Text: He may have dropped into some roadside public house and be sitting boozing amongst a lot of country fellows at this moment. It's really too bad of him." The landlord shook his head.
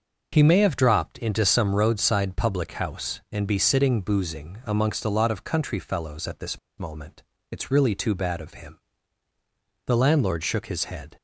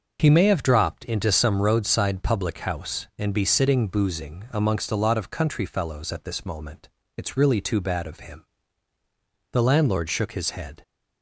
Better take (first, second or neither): second